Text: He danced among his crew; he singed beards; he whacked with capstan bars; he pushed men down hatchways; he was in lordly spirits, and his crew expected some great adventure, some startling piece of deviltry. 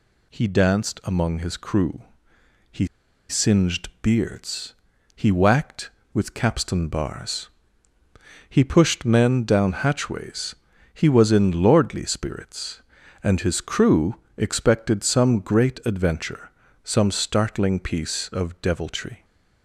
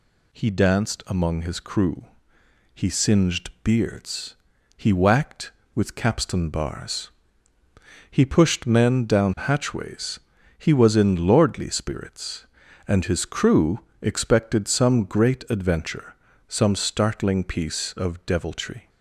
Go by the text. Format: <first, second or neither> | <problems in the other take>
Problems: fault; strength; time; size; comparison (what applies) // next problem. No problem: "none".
second | pauses between "he" and "singed"; at 2.8 s; 0.44 s long // pauses between "crew" and "expected"; slight; at 14.1 s; 0.22 s long; slight in the second